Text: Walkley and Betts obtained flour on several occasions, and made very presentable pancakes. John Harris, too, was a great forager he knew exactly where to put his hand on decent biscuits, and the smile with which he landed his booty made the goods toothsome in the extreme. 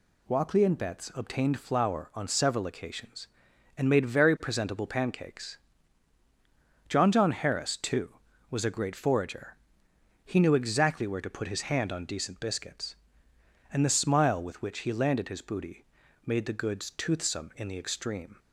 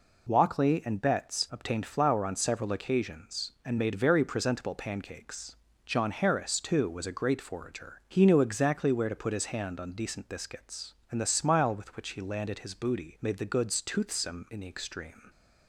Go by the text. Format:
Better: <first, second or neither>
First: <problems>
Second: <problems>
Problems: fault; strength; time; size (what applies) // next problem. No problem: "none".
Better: second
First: says "John" twice; at 7.1 s // pauses between "forager" and "he"; noticeable; at 9.5 s; 0.70 s long // pauses between "booty" and "made"; at 15.8 s; 0.40 s long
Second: none